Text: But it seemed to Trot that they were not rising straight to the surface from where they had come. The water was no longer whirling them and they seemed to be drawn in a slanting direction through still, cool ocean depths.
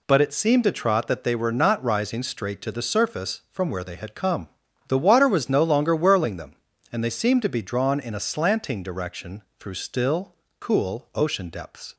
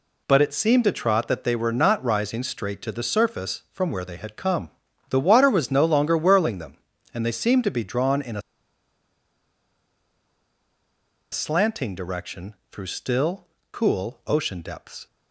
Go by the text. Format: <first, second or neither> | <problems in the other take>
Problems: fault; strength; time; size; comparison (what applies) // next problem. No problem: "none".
first | pauses between "a" and "slanting"; strong; at 8.4 s; 2.9 s long // pauses between "direction" and "through"; slight; at 12.5 s; 0.16 s long; slight in the first